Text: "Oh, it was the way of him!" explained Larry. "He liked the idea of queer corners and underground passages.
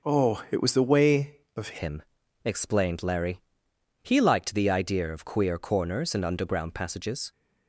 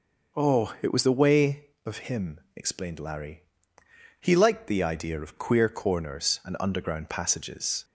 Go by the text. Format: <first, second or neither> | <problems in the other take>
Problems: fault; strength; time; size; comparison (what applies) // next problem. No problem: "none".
second | starts louder than the rest; until 1.1 s; 6.5 dB; noticeable in the second // changes voice at "him"; from 1.7 s on; 5.6 s long